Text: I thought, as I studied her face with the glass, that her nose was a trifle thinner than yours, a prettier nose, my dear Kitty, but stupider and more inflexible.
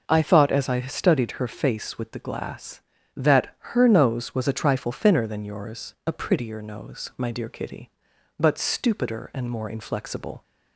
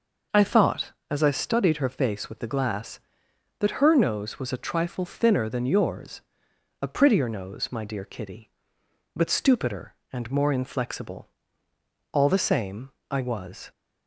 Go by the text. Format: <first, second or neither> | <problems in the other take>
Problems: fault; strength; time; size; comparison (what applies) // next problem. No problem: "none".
first | goes on to say "All the same I was"; from 12.1 s on; 1.5 s long